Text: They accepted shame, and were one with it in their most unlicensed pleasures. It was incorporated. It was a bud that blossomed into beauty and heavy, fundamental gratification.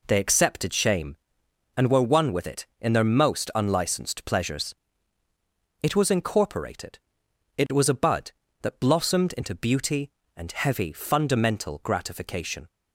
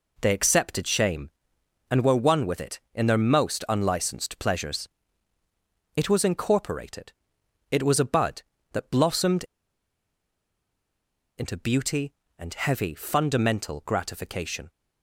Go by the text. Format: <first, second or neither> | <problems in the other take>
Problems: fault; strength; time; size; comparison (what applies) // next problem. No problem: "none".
first | pauses between "blossomed" and "into"; strong; at 9.4 s; 1.9 s long